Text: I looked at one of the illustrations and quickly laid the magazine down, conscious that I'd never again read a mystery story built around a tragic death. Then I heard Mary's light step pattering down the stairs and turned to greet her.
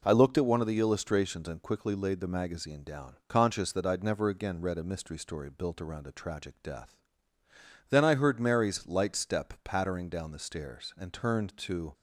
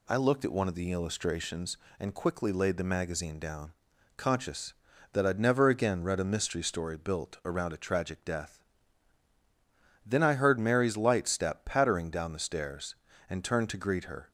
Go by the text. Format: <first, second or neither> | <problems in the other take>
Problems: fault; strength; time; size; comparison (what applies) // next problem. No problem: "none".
second | stops before "greet her"; at 11.9 s